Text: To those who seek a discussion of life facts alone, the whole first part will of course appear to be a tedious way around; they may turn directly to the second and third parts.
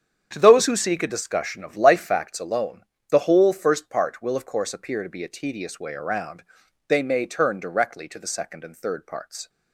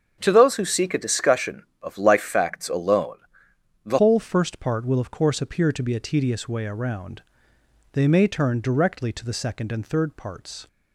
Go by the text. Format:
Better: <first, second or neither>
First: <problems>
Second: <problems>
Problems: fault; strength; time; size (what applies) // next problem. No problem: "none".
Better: first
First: starts louder than the rest; strong; until 1.3 s; 8 dB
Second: starts louder than the rest; strong; until 1.2 s; 7.5 dB // changes voice at "whole"; from 3.9 s on; 6.7 s long